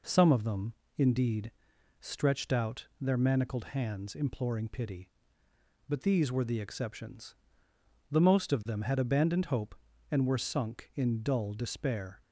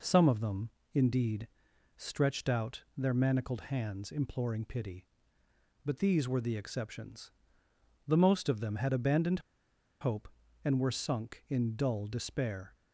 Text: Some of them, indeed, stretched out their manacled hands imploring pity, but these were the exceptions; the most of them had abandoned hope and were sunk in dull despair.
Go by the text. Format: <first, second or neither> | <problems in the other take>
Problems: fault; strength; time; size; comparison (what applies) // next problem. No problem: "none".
first | pauses between "out" and "their"; slight; at 2.8 s; 0.16 s long; slight in the first // pauses between "abandoned" and "hope"; noticeable; at 9.4 s; 0.59 s long